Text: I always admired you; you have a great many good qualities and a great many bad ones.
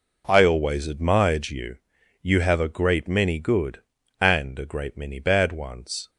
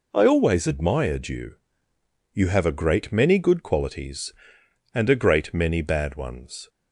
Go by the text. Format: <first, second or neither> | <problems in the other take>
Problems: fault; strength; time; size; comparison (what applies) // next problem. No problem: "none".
second | skips "qualities"; at 4.0 s